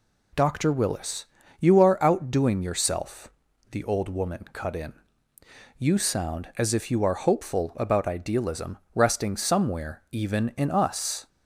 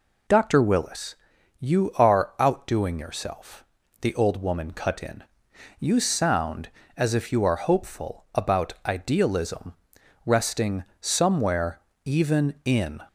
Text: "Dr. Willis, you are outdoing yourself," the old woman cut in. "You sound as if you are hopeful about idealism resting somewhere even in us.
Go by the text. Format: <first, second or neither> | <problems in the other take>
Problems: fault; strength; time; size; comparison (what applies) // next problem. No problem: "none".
first | pauses between "idealism" and "resting"; noticeable; at 9.7 s; 0.50 s long; slight in the first // pauses between "resting" and "somewhere"; slight; at 10.8 s; 0.16 s long // pauses between "somewhere" and "even"; slight; at 11.7 s; 0.24 s long // stops before "us"; at 13.0 s